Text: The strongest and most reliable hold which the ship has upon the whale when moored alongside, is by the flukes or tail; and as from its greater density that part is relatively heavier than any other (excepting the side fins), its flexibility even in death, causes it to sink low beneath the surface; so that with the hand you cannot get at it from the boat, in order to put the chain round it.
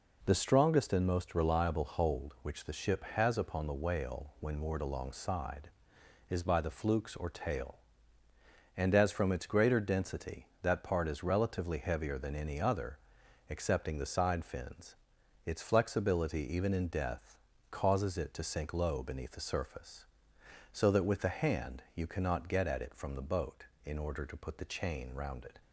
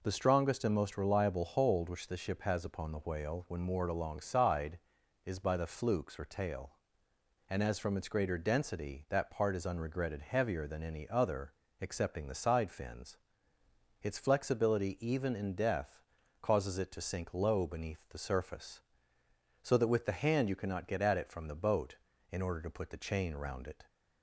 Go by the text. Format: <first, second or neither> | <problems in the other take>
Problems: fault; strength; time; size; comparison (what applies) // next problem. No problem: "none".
first | says "unregretted" for "relatively"; at 9.6 s